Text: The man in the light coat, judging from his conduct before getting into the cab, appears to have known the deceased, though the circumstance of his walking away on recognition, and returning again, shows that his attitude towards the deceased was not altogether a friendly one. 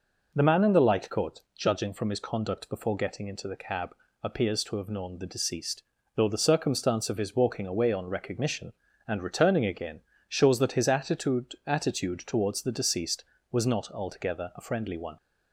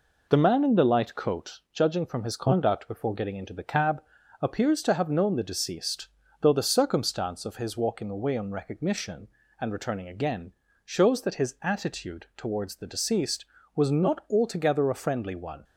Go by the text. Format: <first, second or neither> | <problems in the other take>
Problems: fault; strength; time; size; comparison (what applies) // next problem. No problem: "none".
second | says "attitude" twice; at 11.6 s